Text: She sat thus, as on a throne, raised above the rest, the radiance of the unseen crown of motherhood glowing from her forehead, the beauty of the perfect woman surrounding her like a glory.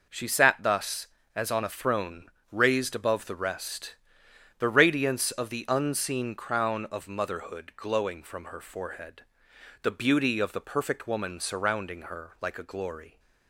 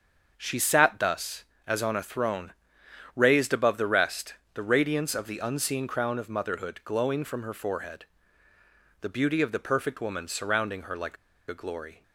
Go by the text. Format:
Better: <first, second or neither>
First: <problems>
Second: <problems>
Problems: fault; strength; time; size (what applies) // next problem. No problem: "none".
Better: first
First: none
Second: starts louder than the rest; until 1.3 s; 7 dB // pauses between "like" and "a"; slight; at 11.1 s; 0.32 s long